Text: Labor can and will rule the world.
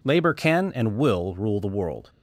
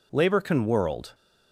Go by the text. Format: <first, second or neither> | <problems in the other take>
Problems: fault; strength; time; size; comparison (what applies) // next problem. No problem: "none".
first | skips "and will rule the"; at 0.6 s